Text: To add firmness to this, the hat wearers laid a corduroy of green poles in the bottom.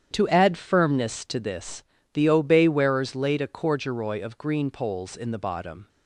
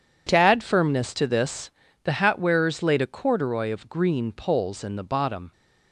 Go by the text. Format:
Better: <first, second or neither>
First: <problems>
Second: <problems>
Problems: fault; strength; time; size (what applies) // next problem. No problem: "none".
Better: second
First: starts louder than the rest; strong; until 1.1 s; 9 dB // says "obey" for "hat"; at 2.2 s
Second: none